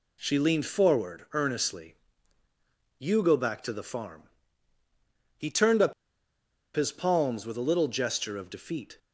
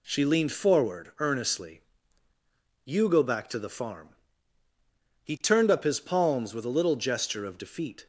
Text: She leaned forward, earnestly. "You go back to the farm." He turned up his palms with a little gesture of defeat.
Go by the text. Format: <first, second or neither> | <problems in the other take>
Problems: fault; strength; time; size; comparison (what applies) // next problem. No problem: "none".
second | pauses between "up" and "his"; noticeable; at 5.9 s; 0.82 s long